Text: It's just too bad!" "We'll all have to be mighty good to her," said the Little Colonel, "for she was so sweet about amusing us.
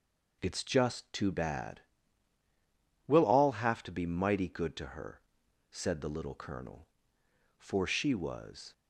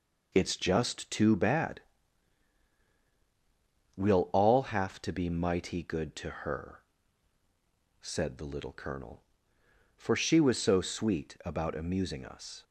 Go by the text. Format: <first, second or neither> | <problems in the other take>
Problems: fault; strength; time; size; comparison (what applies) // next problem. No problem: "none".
second | stops before "so sweet about amusing us"; at 8.7 s